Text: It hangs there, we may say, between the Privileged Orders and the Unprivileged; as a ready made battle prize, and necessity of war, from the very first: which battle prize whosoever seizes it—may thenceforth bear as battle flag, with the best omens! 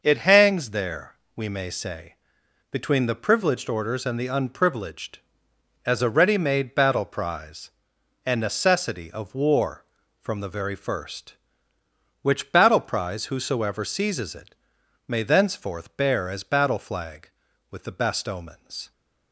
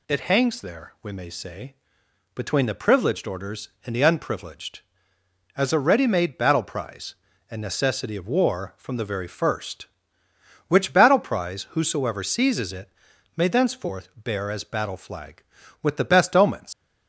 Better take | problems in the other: first | leaves "omens" unfinished; at 16.7 s; 100 ms

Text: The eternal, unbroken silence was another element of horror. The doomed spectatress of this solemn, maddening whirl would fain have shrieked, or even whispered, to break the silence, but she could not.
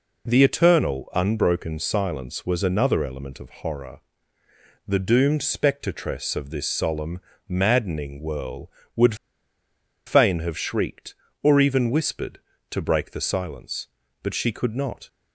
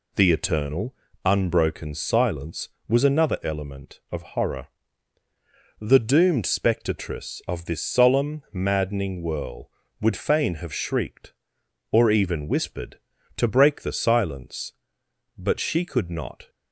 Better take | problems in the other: second | pauses between "would" and "fain"; noticeable; at 9.1 s; 0.92 s long

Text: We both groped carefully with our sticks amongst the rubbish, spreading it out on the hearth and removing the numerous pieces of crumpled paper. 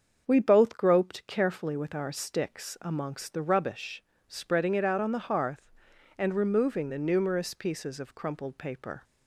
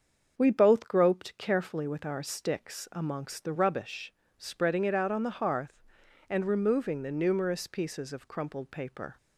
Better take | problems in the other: neither | starts louder than the rest; the same in both

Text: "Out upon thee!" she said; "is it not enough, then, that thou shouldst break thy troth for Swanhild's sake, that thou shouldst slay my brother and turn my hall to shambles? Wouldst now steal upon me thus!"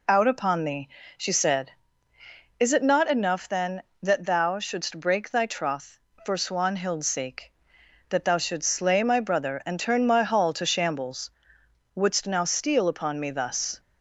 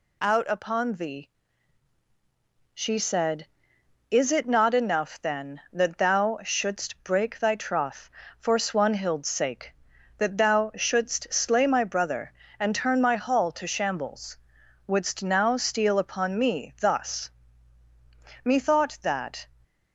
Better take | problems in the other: first | goes on to say "Methought that"; noticeable; from 18.4 s on; 1.0 s long

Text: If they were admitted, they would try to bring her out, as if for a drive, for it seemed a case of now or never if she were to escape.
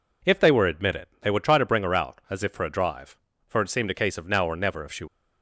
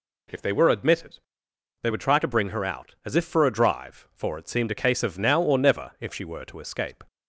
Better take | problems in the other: second | stops before "were to escape"; at 5.0 s

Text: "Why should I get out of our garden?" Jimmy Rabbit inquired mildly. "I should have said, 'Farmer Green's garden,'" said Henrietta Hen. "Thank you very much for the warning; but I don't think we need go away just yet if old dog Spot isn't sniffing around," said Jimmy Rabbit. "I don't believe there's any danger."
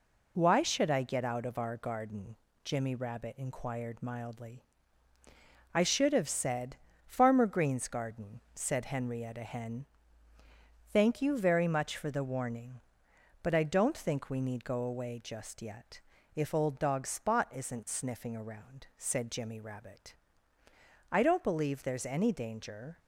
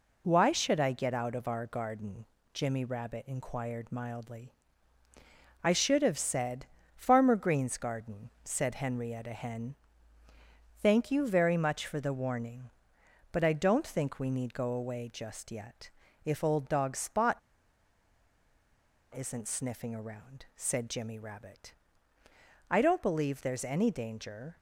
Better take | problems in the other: first | pauses between "yet" and "if"; slight; at 15.9 s; 0.32 s long; slight in the first // pauses between "Spot" and "isn't"; strong; at 17.3 s; 1.7 s long

